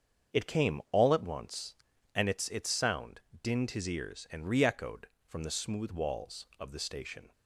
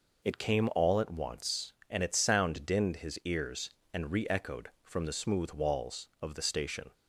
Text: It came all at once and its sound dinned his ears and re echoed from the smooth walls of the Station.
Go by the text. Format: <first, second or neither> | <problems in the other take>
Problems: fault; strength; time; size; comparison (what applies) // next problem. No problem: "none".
second | starts louder than the rest; until 1.4 s; 7 dB // says "its" twice; at 2.4 s // pauses between "sound" and "dinned"; slight; at 3.1 s; 0.22 s long